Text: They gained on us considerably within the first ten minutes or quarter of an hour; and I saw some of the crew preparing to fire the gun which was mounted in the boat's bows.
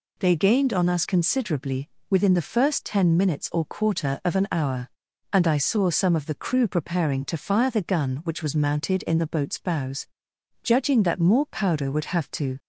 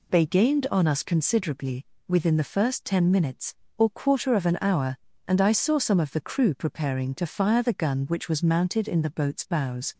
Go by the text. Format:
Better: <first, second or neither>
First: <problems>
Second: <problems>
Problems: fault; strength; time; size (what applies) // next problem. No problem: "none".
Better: second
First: pauses between "considerably" and "within"; slight; at 1.8 s; 0.20 s long // goes on to say "Judging that more powder would have to"; strong; from 10.6 s on; 1.9 s long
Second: pauses between "considerably" and "within"; slight; at 1.8 s; 0.24 s long